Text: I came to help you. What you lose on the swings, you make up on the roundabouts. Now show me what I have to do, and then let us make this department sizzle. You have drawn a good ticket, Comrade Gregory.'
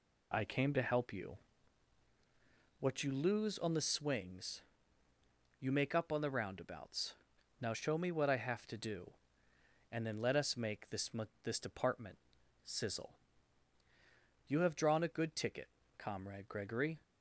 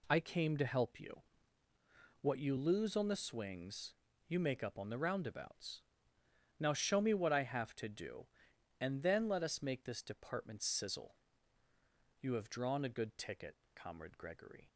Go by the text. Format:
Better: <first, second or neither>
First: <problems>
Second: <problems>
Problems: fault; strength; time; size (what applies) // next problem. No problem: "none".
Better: second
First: says "this" twice; at 11.4 s // pauses between "department" and "sizzle"; noticeable; at 12.1 s; 0.48 s long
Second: none